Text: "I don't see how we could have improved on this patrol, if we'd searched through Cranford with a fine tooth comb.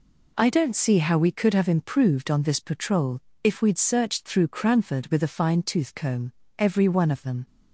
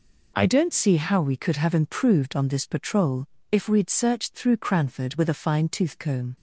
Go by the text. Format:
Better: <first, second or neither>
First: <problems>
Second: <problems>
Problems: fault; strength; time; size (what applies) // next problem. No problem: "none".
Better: second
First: goes on to say "Every one of them"; noticeable; from 6.5 s on; 0.88 s long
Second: none